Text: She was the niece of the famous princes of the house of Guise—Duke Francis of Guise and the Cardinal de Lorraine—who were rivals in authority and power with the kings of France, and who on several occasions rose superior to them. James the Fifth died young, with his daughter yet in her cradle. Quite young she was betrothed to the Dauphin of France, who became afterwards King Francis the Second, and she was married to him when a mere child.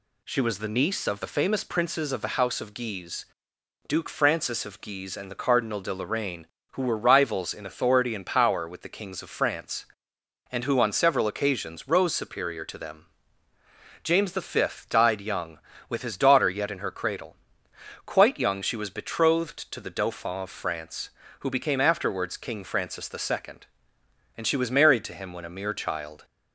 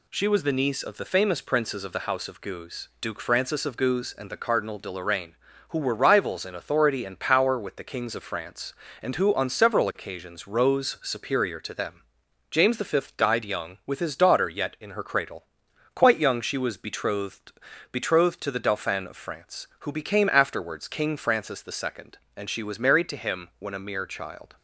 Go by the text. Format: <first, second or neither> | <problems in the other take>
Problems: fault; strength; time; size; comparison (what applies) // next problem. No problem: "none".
first | says "betrothed" twice; at 17.9 s